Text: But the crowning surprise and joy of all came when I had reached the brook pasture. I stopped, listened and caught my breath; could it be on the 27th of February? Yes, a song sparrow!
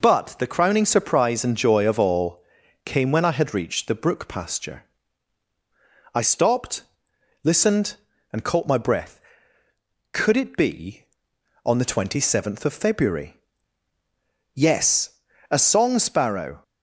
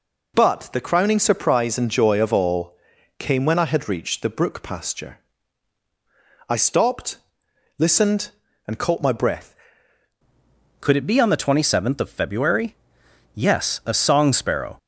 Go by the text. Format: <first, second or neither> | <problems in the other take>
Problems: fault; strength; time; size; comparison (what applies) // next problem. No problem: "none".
first | pauses between "all" and "came"; at 2.7 s; 0.44 s long; also in the first // changes voice at "could"; from 10.7 s on; 4.0 s long